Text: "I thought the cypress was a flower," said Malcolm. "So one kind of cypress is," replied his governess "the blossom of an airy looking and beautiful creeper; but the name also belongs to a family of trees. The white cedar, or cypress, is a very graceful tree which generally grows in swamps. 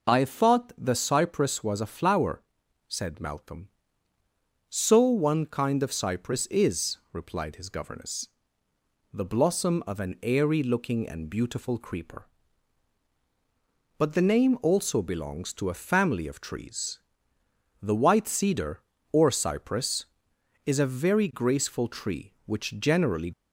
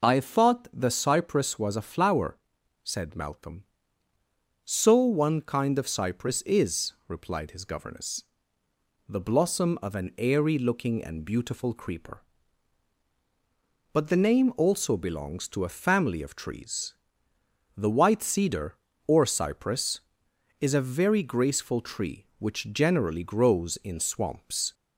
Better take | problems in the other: second | pauses between "governess" and "the"; noticeable; at 8.2 s; 0.86 s long; noticeable in the second // stops before "grows in swamps"; at 23.3 s

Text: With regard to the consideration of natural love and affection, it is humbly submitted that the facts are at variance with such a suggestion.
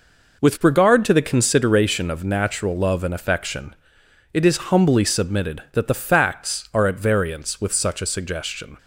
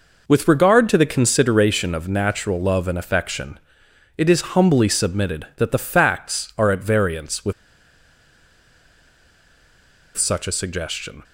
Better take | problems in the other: first | pauses between "with" and "such"; strong; at 7.5 s; 2.6 s long

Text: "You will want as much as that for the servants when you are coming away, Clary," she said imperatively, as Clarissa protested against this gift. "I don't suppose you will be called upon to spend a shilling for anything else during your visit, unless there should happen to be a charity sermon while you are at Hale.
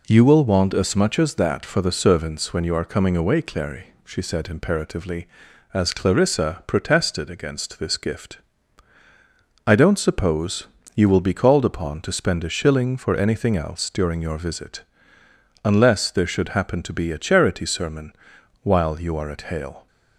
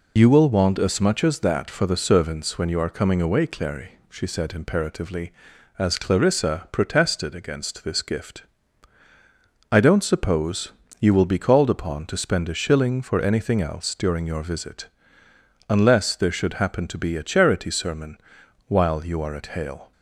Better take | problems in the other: first | loses the start of "You"; at 0.1 s; 45 ms // pauses between "suppose" and "you"; slight; at 10.7 s; 0.28 s long; slight in the first // pauses between "sermon" and "while"; noticeable; at 18.1 s; 0.50 s long; noticeable in the first

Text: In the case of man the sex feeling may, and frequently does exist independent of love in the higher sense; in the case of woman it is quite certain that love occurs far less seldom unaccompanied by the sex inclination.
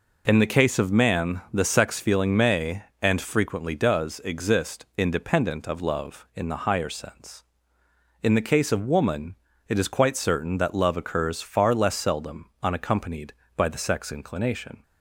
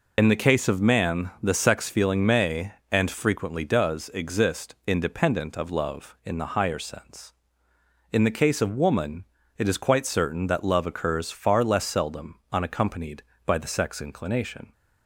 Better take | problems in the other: first | loses the start of "In"; at 0.1 s; 35 ms // pauses between "woman" and "it"; slight; at 9.2 s; 0.32 s long; slight in the first

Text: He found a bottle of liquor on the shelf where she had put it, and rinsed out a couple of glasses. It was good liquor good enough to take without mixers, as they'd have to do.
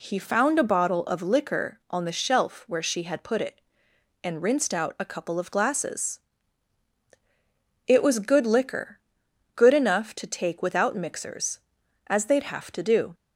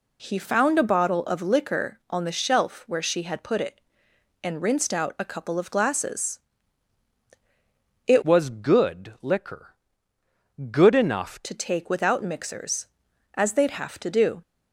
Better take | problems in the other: first | changes voice from "was" to "enough"; from 8.2 to 11.4 s; 3.2 s long // pauses between "liquor" and "good"; noticeable; at 9.7 s; 0.98 s long; noticeable in the first

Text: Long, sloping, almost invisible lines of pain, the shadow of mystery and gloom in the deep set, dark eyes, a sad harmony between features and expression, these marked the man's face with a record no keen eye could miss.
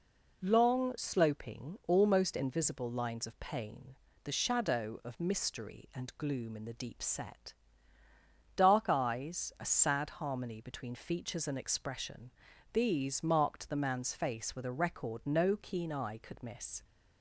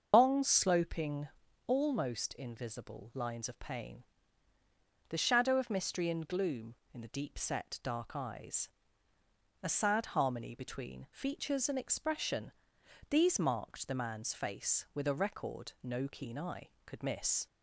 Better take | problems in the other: first | loses the start of "Long"; at 0.1 s; 155 ms // starts louder than the rest; until 1.1 s; 6.5 dB

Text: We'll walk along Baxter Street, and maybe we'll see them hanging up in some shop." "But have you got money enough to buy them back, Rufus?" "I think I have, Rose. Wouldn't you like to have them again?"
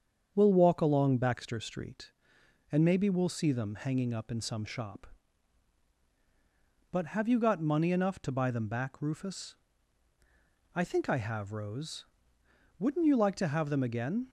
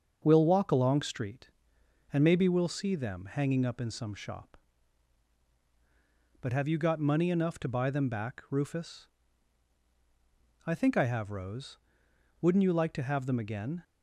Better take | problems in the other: first | starts louder than the rest; until 1.2 s; 6.5 dB; strong in the first // skips "Baxter"; at 1.0 s

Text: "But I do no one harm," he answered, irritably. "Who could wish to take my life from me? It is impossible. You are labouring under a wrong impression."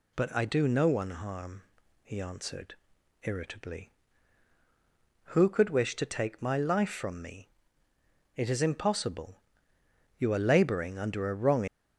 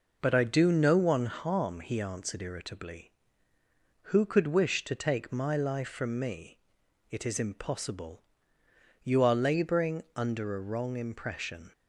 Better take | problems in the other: second | stops before "impression"; at 11.6 s

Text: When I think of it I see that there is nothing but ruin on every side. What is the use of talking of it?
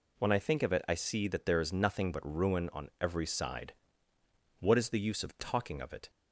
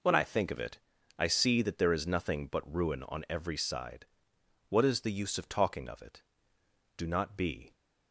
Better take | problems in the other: first | pauses between "it" and "I"; at 0.7 s; 0.40 s long // goes on to say "Do not be"; noticeable; from 6.9 s on; 0.76 s long

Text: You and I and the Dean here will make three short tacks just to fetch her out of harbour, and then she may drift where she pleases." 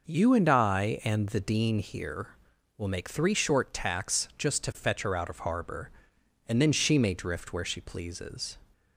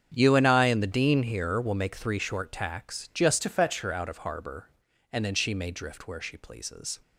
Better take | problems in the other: first | starts louder than the rest; strong; until 1.1 s; 7.5 dB // changes voice from "to" to "fetch"; from 3.4 to 3.8 s; 0.4 s long

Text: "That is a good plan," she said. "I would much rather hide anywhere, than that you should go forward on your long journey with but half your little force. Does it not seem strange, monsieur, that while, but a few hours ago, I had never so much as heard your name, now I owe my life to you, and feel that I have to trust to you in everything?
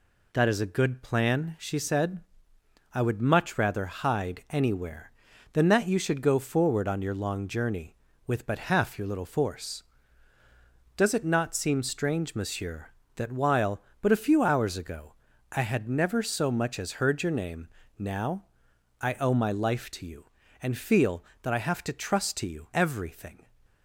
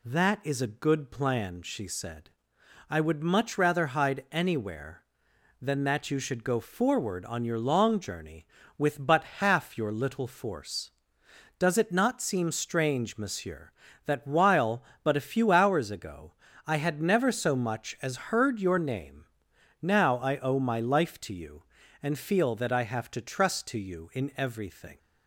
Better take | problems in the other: second | pauses between "now" and "I"; noticeable; at 18.4 s; 0.58 s long // skips "in"; at 22.7 s

